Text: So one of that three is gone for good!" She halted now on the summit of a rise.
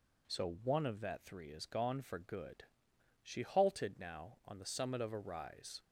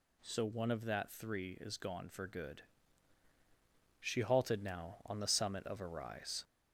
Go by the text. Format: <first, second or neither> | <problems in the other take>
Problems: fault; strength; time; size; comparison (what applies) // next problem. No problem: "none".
first | gets louder; slight; throughout; 2.5 dB